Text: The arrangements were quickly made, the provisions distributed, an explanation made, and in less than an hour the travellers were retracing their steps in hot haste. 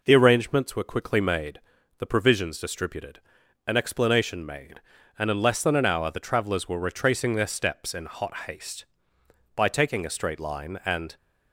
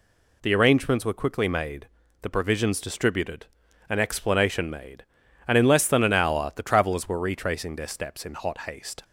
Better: second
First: goes on to say "By taking a straight line and"; from 9.5 s on; 1.6 s long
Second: none

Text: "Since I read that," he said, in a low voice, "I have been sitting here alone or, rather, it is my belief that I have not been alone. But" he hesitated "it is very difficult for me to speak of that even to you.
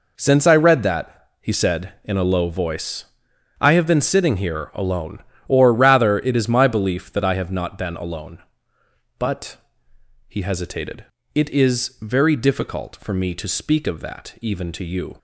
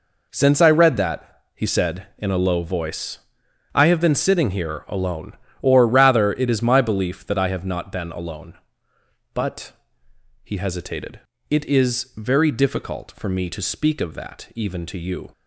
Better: neither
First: pauses between "But" and "he"; noticeable; at 9.5 s; 0.70 s long // pauses between "hesitated" and "it"; slight; at 11.0 s; 0.30 s long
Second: pauses between "But" and "he"; noticeable; at 9.7 s; 0.70 s long // pauses between "hesitated" and "it"; slight; at 11.1 s; 0.30 s long

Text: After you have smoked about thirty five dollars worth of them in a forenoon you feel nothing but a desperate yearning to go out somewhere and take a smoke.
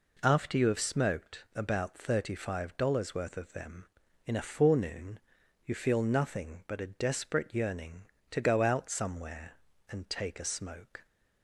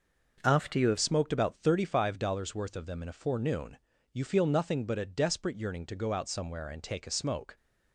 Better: first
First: pauses between "forenoon" and "you"; at 5.1 s; 0.44 s long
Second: changes voice at "smoked"; from 0.9 s on; 6.6 s long // pauses between "forenoon" and "you"; slight; at 3.7 s; 0.34 s long

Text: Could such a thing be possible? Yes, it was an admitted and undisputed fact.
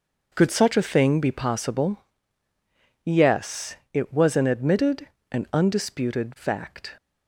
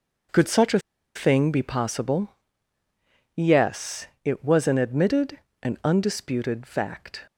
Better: first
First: none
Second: pauses between "a" and "thing"; at 0.7 s; 0.36 s long

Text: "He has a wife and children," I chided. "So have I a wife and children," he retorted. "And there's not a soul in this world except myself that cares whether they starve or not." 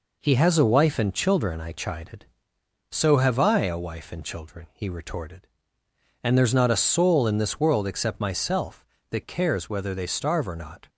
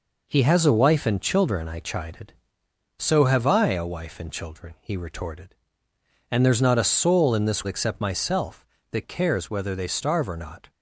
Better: first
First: none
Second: skips "world"; at 7.6 s

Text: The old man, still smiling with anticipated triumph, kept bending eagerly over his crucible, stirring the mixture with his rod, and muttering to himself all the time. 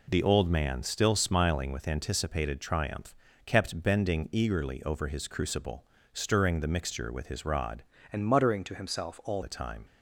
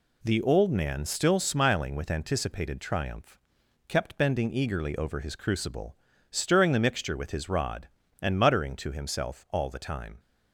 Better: second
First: changes voice from "and" to "all"; from 8.1 to 9.4 s; 1.3 s long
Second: none

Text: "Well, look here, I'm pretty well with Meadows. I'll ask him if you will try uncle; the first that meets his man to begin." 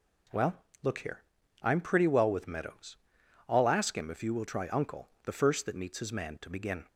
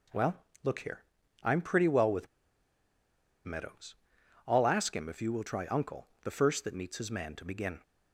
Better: first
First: none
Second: pauses between "with" and "Meadows"; at 2.2 s; 1.1 s long

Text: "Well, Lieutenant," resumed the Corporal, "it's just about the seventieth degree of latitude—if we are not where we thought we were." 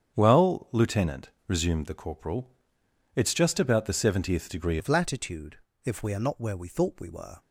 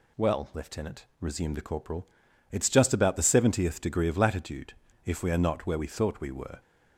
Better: second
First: starts louder than the rest; strong; until 1.2 s; 8 dB // changes voice at "of"; from 4.7 s on; 2.7 s long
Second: none

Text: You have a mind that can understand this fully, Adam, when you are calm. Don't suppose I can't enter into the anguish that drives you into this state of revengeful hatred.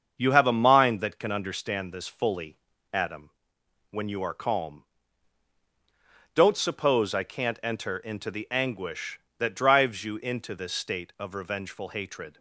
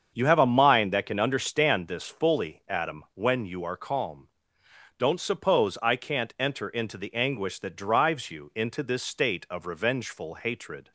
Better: neither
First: starts louder than the rest; until 1.2 s; 7 dB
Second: starts louder than the rest; strong; until 1.1 s; 7 dB

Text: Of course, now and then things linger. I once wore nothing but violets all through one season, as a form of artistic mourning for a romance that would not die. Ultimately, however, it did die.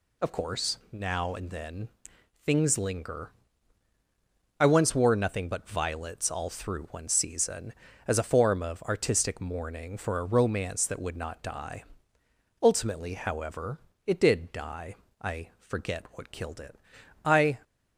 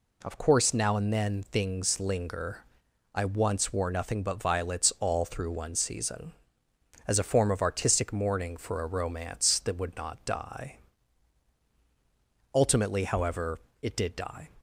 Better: second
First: pauses between "then" and "things"; noticeable; at 1.8 s; 0.56 s long // goes on to say "I forget what killed it I"; strong; from 15.2 s on; 2.3 s long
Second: none

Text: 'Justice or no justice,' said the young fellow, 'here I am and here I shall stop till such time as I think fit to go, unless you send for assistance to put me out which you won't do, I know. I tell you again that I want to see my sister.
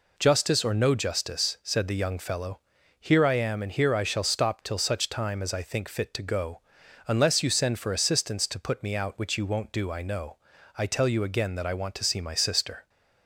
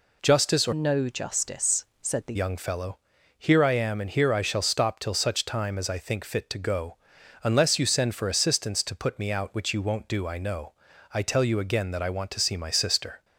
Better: first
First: none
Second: changes voice from "no" to "the"; from 0.7 to 2.3 s; 1.6 s long

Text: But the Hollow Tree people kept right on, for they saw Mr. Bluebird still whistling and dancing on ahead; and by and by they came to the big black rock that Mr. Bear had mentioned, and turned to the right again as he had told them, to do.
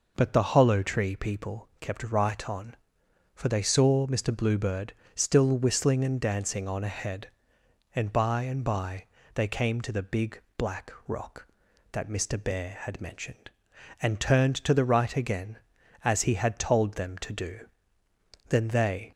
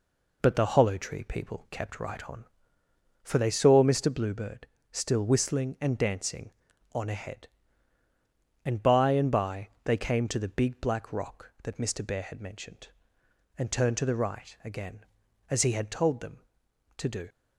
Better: second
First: pauses between "Bluebird" and "still"; slight; at 4.9 s; 0.20 s long // pauses between "by" and "they"; slight; at 9.0 s; 0.30 s long // pauses between "big" and "black"; slight; at 10.3 s; 0.18 s long // pauses between "black" and "rock"; slight; at 10.9 s; 0.16 s long // goes on to say "Then they"; noticeable; from 18.4 s on; 0.62 s long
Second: pauses between "Bluebird" and "still"; slight; at 4.6 s; 0.24 s long // pauses between "by" and "they"; slight; at 9.6 s; 0.16 s long

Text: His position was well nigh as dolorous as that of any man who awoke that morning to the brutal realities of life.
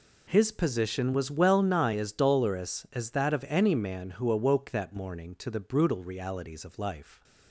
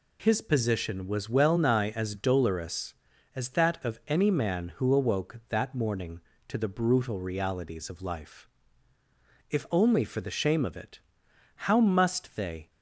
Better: first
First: none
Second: goes on to say "If only for the shame of it How must they"; strong; from 9.4 s on; 3.2 s long

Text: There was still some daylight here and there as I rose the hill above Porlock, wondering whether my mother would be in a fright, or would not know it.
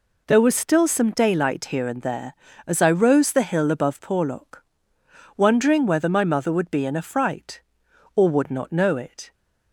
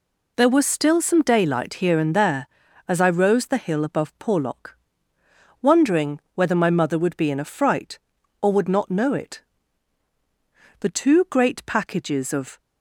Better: first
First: none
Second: pauses between "wondering" and "whether"; slight; at 6.1 s; 0.16 s long // goes on to say "The two great packages of"; strong; from 10.8 s on; 1.7 s long

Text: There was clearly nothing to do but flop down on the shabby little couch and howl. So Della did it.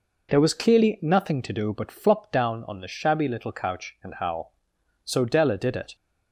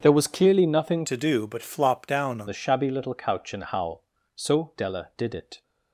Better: first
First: none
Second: starts louder than the rest; strong; until 1.0 s; 7.5 dB // changes voice from "to" to "on"; from 1.0 to 2.4 s; 1.4 s long

